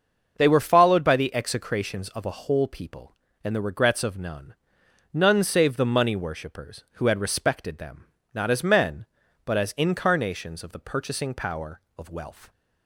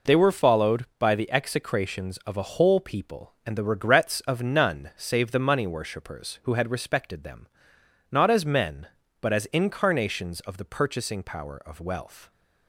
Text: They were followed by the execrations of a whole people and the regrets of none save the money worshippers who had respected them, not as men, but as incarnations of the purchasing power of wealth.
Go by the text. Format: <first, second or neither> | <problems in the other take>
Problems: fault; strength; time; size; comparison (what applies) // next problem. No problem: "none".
second | starts louder than the rest; until 1.3 s; 6.5 dB // says "none" twice; at 5.1 s